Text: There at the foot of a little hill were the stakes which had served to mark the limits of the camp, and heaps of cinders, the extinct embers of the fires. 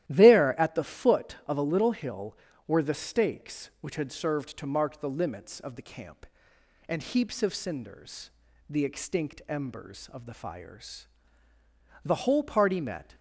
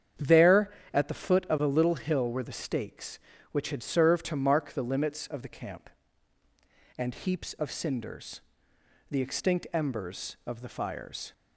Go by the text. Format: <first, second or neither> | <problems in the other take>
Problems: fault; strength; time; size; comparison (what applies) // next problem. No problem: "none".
second | starts louder than the rest; strong; until 1.1 s; 13 dB; strong in the second // goes on to say "The whole party met"; noticeable; from 12.0 s on; 1.1 s long